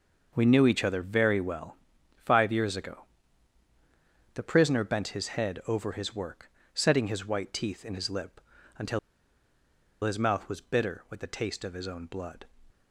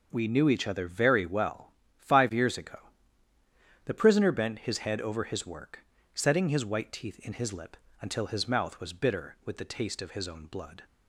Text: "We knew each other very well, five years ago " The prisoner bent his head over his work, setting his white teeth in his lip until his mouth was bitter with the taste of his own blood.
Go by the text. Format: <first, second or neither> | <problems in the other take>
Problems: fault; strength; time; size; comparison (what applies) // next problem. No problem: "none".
second | pauses between "lip" and "until"; slight; at 8.3 s; 0.36 s long; slight in the second // pauses between "until" and "his"; at 8.9 s; 1.0 s long